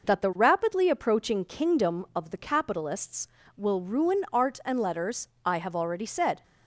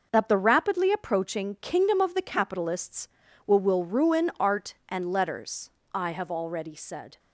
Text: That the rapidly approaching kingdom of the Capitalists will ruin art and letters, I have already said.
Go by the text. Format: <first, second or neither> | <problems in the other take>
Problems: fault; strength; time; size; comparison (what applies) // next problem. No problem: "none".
first | says "will" twice; at 3.5 s